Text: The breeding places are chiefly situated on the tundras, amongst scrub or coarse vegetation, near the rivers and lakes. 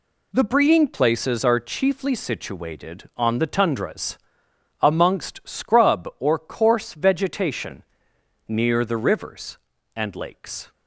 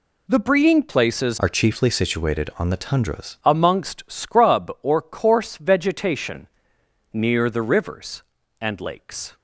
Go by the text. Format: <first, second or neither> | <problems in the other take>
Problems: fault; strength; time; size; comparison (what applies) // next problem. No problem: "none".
first | changes voice from "are" to "tundras"; from 1.3 to 3.3 s; 2.0 s long